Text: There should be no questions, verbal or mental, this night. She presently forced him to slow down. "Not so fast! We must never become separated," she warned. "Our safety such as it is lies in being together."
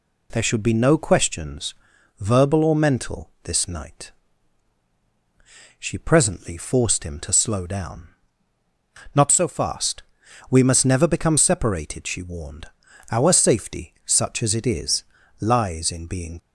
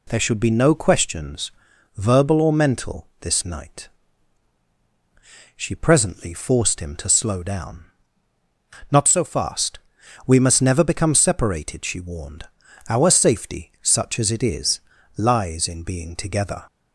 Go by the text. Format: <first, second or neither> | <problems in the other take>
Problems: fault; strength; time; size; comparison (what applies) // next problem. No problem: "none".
second | pauses between "is" and "lies"; slight; at 15.0 s; 0.36 s long; slight in the second // stops before "together"; at 16.3 s